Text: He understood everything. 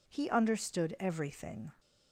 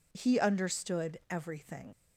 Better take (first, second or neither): first